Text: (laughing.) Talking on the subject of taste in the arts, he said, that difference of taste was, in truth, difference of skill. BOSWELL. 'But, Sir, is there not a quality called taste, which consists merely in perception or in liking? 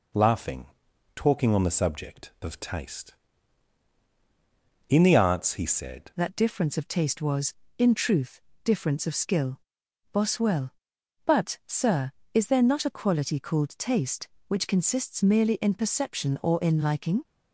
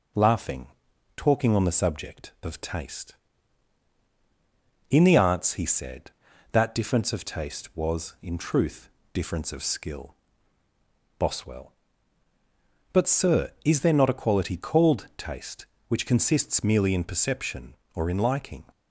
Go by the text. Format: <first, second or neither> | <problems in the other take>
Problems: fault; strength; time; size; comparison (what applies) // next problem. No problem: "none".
second | changes voice at "that"; from 6.1 s on; 11.1 s long